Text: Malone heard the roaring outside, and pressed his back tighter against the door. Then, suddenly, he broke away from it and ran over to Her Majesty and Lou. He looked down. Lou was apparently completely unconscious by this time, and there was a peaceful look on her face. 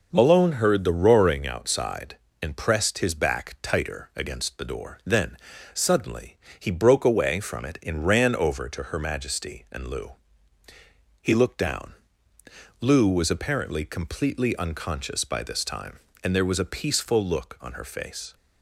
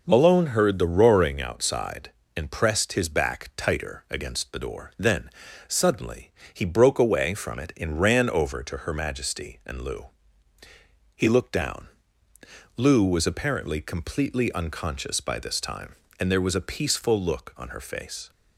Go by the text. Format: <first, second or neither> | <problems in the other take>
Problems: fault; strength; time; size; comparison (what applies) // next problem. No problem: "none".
neither | none